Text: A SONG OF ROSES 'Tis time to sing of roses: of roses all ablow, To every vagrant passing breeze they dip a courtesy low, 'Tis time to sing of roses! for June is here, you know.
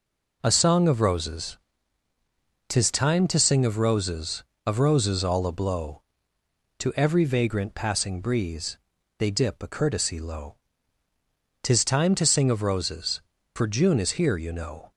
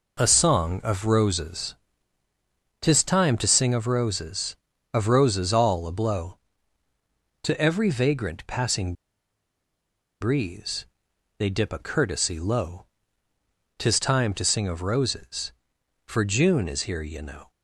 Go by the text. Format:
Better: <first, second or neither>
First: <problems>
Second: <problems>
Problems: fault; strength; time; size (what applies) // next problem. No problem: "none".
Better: first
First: pauses between "ROSES" and "Tis"; at 1.5 s; 1.1 s long // pauses between "breeze" and "they"; at 8.7 s; 0.40 s long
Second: pauses between "ROSES" and "Tis"; at 1.7 s; 1.0 s long // pauses between "passing" and "breeze"; strong; at 8.9 s; 1.2 s long // pauses between "breeze" and "they"; noticeable; at 10.8 s; 0.50 s long